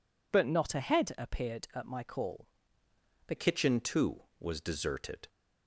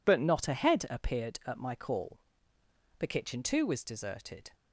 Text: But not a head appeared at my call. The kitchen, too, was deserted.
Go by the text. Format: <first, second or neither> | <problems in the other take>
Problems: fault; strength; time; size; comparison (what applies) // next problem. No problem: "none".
second | changes voice at "kitchen"; from 3.3 s on; 1.9 s long